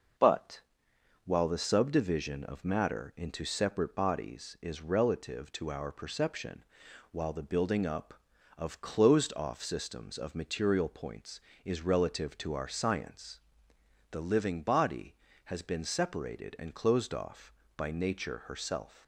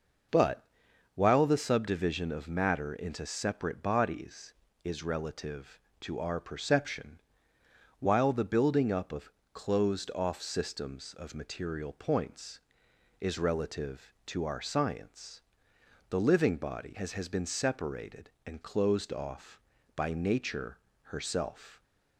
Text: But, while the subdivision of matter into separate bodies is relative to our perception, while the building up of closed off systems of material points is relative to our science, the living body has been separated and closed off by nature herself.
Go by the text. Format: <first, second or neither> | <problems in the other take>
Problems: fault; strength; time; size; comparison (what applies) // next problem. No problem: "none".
first | pauses between "of" and "closed"; slight; at 9.3 s; 0.20 s long // says "has" twice; at 17.1 s // pauses between "nature" and "herself"; slight; at 20.7 s; 0.24 s long